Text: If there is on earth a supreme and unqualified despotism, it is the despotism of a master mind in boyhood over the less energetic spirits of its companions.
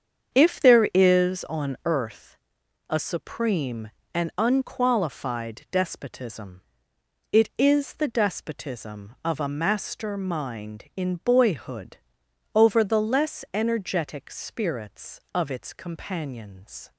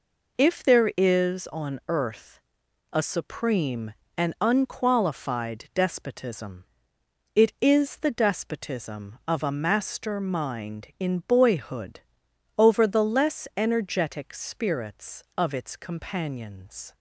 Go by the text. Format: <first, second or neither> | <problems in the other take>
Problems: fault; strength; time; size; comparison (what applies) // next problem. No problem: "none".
second | starts louder than the rest; strong; until 2.0 s; 7.5 dB // pauses between "earth" and "a"; noticeable; at 2.3 s; 0.52 s long; noticeable in the second // pauses between "boyhood" and "over"; noticeable; at 11.9 s; 0.58 s long; noticeable in the second